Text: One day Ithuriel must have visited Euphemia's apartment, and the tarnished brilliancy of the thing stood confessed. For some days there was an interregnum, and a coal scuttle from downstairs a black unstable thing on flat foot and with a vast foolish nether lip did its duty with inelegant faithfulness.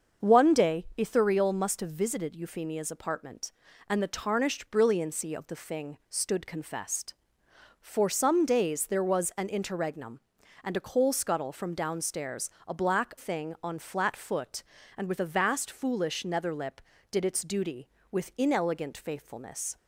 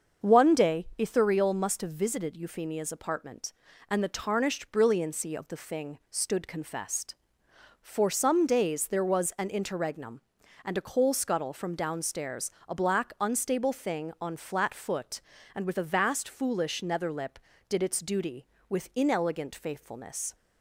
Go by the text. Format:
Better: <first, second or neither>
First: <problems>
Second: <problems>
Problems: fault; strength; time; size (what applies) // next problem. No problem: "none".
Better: second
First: starts louder than the rest; until 1.3 s; 6.5 dB // pauses between "downstairs" and "a"; slight; at 12.5 s; 0.16 s long // skips "unstable"; at 13.1 s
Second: starts louder than the rest; until 1.3 s; 6.5 dB // pauses between "downstairs" and "a"; slight; at 12.5 s; 0.16 s long